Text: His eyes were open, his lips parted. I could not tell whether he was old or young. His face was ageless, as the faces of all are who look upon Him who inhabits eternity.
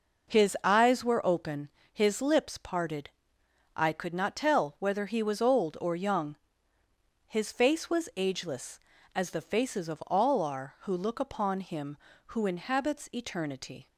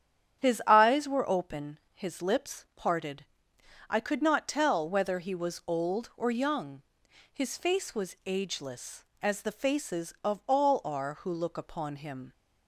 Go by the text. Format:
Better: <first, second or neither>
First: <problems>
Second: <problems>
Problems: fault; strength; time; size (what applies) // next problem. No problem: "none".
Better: first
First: none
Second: starts louder than the rest; strong; until 1.4 s; 9 dB // stops before "who inhabits eternity"; at 12.3 s